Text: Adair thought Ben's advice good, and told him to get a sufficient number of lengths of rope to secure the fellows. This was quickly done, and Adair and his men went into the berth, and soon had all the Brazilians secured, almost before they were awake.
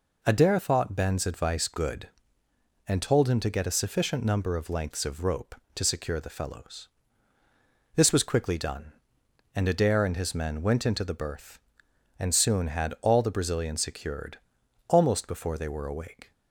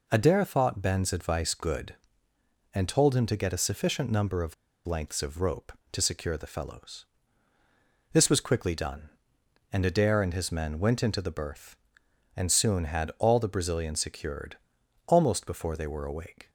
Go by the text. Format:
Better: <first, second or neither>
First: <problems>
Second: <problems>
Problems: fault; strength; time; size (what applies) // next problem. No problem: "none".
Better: first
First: none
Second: pauses between "of" and "lengths"; slight; at 4.5 s; 0.31 s long